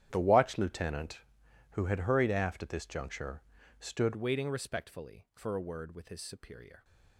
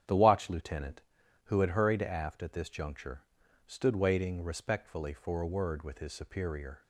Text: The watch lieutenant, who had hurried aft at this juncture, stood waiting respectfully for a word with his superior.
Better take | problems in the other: second | starts louder than the rest; strong; until 1.1 s; 10.5 dB; strong in the second // changes voice at "waiting"; from 4.1 s on; 2.7 s long

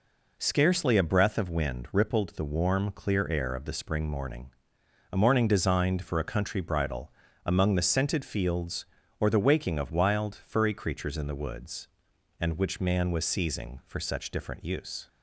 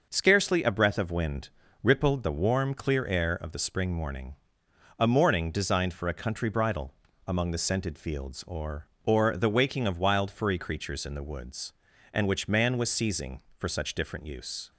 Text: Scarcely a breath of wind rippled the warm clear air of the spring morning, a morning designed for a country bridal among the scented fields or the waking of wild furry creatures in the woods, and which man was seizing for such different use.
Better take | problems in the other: first | starts louder than the rest; noticeable; until 1.1 s; 6 dB // pauses between "wind" and "rippled"; slight; at 1.5 s; 0.32 s long // pauses between "bridal" and "among"; slight; at 6.9 s; 0.32 s long; slight in the first // says "or" twice; at 9.0 s

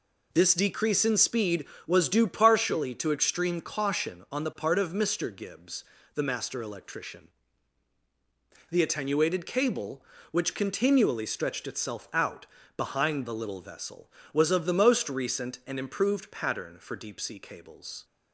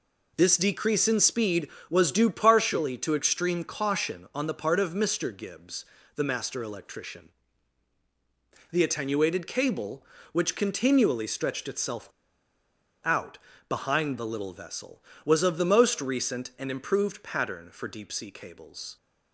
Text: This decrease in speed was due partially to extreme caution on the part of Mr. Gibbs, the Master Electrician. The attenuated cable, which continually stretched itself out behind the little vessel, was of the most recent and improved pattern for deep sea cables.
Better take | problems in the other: first | pauses between "itself" and "out"; noticeable; at 12.0 s; 0.96 s long // pauses between "out" and "behind"; slight; at 13.3 s; 0.32 s long; slight in the first

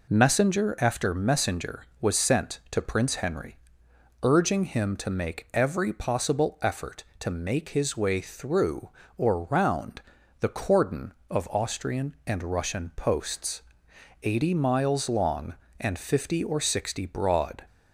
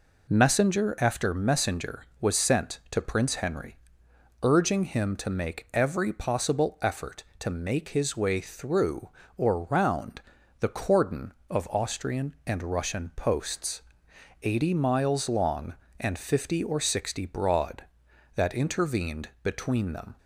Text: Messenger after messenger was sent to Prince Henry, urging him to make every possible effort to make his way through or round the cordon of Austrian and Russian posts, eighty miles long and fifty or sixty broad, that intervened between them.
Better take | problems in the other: second | pauses between "round" and "the"; at 9.9 s; 0.40 s long; also in the second // stops before "that intervened between them"; at 17.6 s

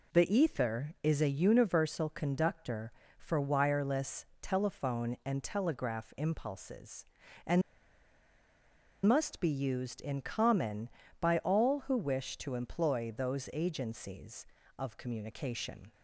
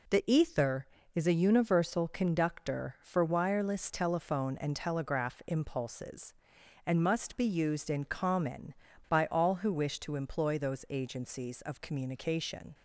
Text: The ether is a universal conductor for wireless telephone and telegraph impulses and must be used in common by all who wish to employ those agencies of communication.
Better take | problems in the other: second | pauses between "wireless" and "telephone"; slight; at 4.2 s; 0.18 s long // pauses between "and" and "must"; strong; at 7.6 s; 1.4 s long

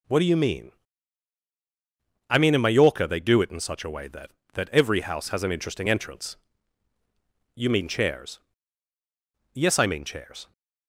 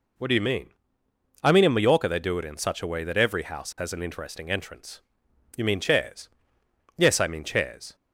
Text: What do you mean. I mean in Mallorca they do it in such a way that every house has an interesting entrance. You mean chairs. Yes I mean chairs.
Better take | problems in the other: second | says "that" twice; at 4.5 s

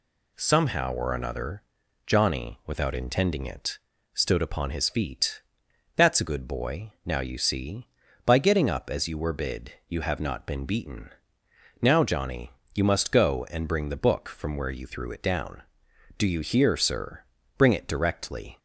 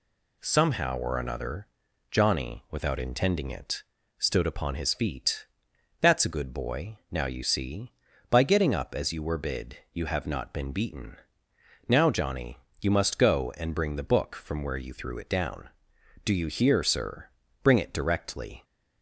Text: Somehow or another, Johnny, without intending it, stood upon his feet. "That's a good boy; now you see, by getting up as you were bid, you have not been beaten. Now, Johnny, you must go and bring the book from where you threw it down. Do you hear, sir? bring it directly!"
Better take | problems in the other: neither | none

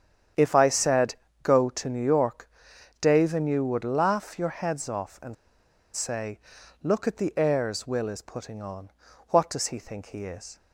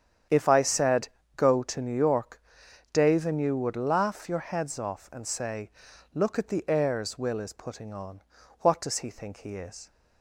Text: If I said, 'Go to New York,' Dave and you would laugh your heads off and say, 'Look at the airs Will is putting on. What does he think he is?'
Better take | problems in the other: second | starts louder than the rest; strong; until 1.6 s; 8.5 dB; strong in the second // pauses between "and" and "say"; noticeable; at 5.3 s; 0.60 s long

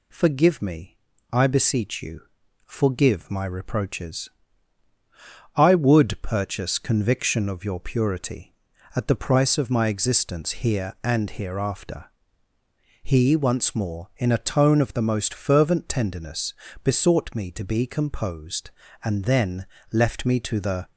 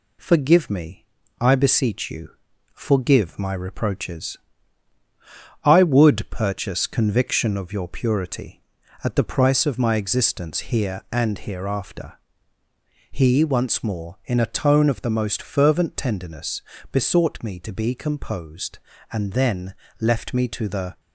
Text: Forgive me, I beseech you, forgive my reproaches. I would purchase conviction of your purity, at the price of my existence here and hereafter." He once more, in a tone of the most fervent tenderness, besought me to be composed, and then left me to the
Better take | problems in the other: first | gets quieter; slight; throughout; 2 dB // pauses between "then" and "left"; slight; at 19.7 s; 0.24 s long; slight in the first

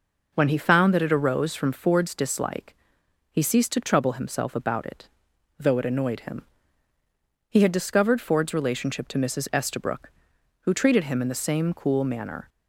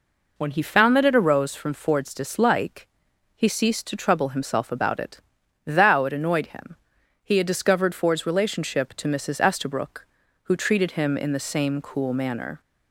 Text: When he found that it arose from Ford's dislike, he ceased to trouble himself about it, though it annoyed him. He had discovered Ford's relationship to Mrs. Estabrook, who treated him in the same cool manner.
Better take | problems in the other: first | says "thou" for "though"; at 5.6 s

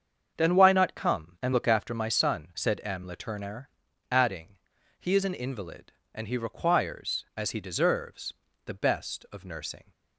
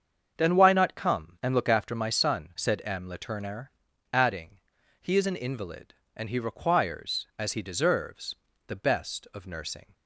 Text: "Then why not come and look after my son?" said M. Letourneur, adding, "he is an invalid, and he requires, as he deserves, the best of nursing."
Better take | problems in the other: neither | starts louder than the rest; the same in both

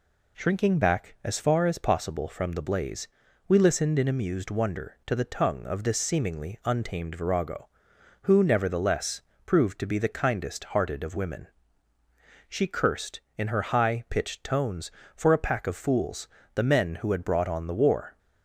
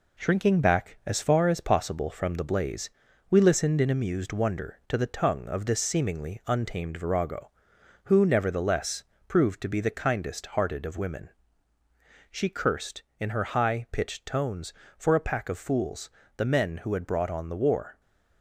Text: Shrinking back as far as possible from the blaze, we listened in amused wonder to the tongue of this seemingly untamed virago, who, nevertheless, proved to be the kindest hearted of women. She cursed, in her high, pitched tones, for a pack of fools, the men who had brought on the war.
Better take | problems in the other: first | gets quieter; noticeable; throughout; 4 dB

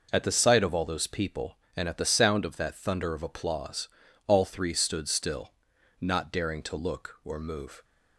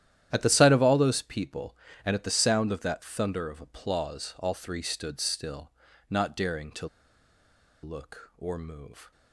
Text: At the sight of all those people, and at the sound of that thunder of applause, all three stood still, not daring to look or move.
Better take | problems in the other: first | starts louder than the rest; strong; until 1.3 s; 11.5 dB // pauses between "to" and "look"; noticeable; at 6.8 s; 0.96 s long

